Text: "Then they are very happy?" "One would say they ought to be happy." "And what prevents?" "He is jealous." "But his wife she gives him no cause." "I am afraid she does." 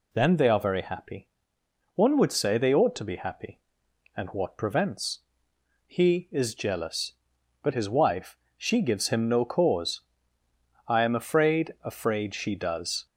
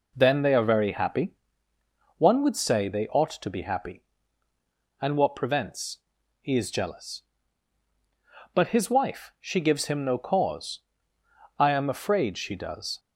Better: second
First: pauses between "wife" and "she"; slight; at 8.3 s; 0.20 s long // says "afraid" twice; at 11.8 s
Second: none

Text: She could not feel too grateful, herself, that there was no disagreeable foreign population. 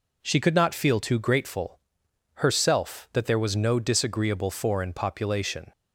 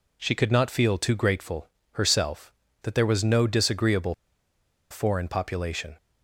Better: first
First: none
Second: pauses between "disagreeable" and "foreign"; noticeable; at 4.1 s; 0.78 s long

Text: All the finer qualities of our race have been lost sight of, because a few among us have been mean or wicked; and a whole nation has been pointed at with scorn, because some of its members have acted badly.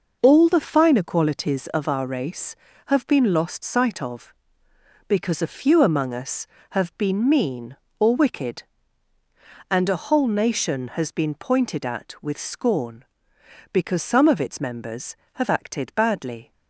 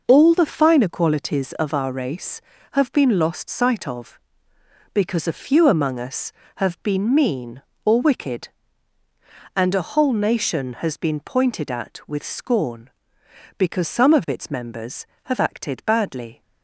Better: neither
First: none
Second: none

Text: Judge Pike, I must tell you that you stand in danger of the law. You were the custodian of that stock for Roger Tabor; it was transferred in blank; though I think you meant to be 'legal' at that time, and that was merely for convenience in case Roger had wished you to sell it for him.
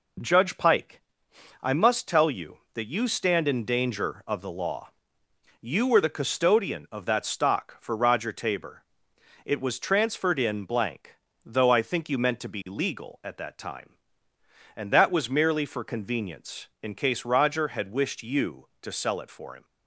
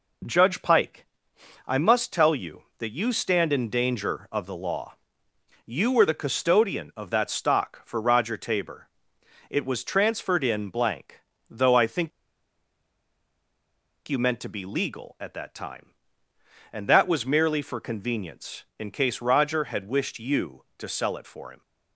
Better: first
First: none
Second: pauses between "think" and "you"; strong; at 12.1 s; 1.9 s long

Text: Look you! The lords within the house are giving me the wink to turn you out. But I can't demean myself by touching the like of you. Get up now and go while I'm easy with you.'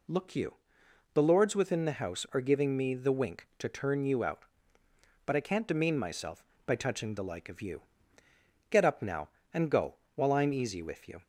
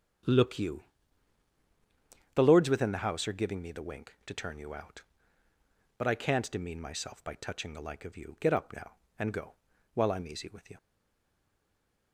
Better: first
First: pauses between "go" and "while"; slight; at 9.9 s; 0.20 s long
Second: starts louder than the rest; strong; until 2.7 s; 8 dB // pauses between "go" and "while"; at 9.5 s; 0.42 s long // stays silent after the last word; noticeable; from 10.7 s on; 1.4 s long

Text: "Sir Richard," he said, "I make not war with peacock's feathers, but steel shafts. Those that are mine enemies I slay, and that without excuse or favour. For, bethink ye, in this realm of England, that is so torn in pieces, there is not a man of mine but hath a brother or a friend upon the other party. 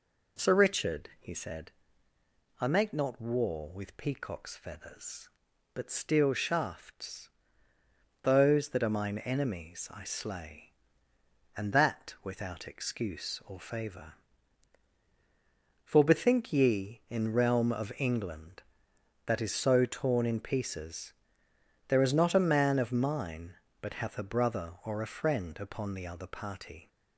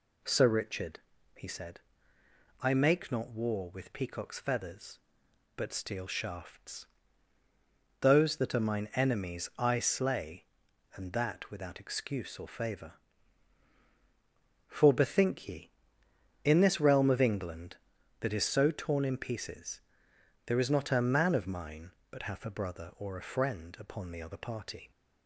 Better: second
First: skips "this"; at 17.3 s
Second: none

